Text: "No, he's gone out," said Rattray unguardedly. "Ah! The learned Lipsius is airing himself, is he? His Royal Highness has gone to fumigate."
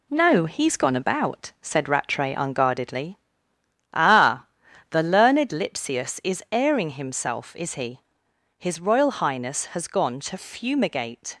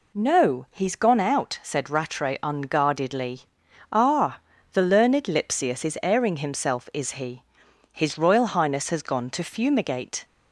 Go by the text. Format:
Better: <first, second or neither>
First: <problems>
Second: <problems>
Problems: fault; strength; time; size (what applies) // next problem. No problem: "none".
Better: second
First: says "about" for "out"; at 0.9 s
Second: none